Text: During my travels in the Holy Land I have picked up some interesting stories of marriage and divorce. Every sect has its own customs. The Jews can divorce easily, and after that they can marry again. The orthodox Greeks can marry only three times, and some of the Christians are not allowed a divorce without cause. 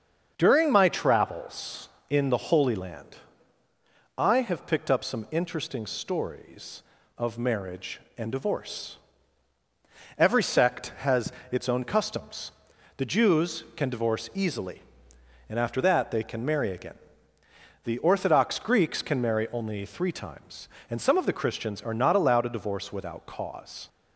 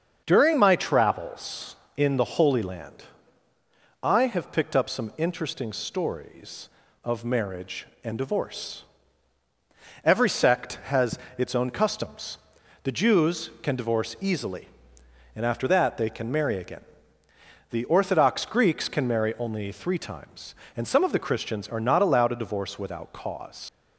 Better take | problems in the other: first | starts louder than the rest; until 1.2 s; 7 dB; also in the first // pauses between "Land" and "I"; at 3.0 s; 1.0 s long; also in the first // pauses between "has" and "its"; slight; at 11.1 s; 0.20 s long; slight in the first // leaves "cause" unfinished; at 23.6 s; 55 ms

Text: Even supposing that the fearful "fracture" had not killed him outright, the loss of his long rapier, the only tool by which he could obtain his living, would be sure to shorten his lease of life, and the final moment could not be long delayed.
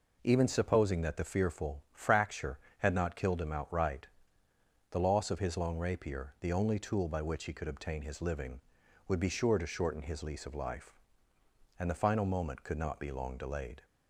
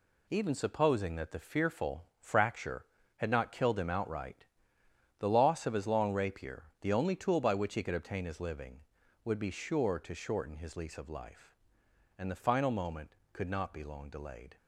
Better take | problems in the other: first | gets quieter; throughout; 7 dB // pauses between "fearful" and "fracture"; slight; at 2.0 s; 0.16 s long

